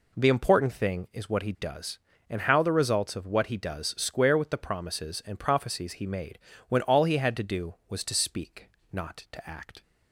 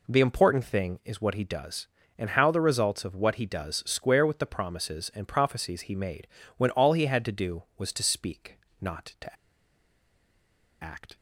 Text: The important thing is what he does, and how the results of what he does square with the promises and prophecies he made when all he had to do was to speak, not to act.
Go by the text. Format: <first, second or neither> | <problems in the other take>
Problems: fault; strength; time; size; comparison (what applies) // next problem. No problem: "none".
first | pauses between "made" and "when"; slight; at 6.2 s; 0.30 s long; slight in the first // pauses between "to" and "act"; strong; at 9.3 s; 1.4 s long